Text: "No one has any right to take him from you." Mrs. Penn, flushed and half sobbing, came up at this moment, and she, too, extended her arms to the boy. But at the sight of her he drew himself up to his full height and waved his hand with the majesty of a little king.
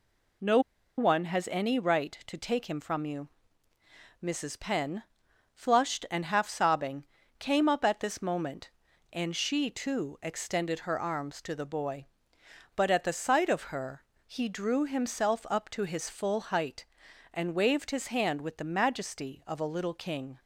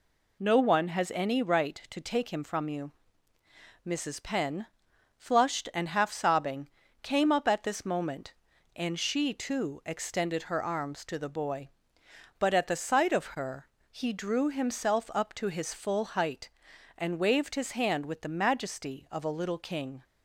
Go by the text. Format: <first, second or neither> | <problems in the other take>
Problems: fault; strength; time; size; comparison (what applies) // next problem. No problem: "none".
second | pauses between "No" and "one"; at 0.5 s; 0.38 s long // pauses between "her" and "he"; slight; at 14.0 s; 0.22 s long; slight in the second